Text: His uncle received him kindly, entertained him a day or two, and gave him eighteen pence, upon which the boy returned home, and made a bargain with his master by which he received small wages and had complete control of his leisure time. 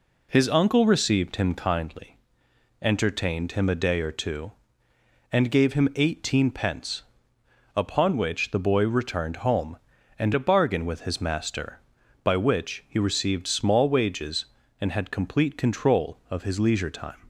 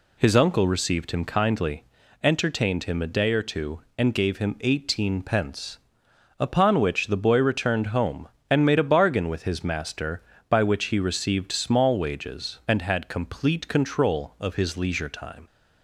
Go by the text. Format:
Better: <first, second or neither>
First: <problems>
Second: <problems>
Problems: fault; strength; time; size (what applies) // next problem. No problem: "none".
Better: second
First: skips "made"; at 10.3 s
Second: none